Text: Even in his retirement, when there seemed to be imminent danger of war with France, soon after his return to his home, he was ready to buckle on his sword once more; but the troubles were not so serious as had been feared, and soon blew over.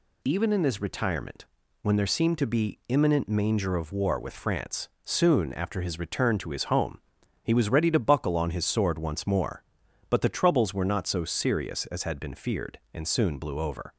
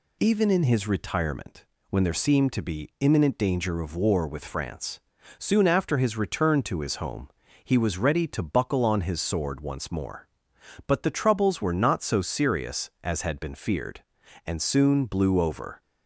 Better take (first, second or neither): second